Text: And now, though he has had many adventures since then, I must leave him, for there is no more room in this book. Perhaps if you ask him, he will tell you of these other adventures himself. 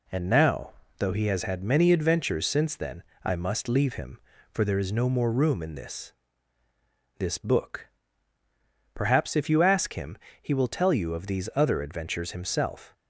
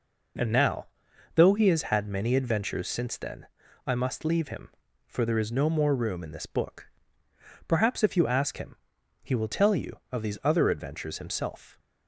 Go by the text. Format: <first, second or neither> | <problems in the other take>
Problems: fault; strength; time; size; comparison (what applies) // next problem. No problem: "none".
second | says "this" twice; at 7.1 s